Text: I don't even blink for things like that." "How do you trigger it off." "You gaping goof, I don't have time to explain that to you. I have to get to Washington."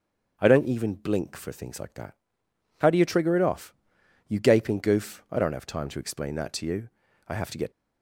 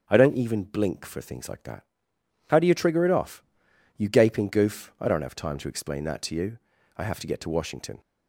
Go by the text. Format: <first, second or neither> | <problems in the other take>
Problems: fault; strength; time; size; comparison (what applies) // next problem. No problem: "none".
second | starts louder than the rest; until 1.3 s; 6.5 dB; also in the second // stops before "to Washington"; at 7.7 s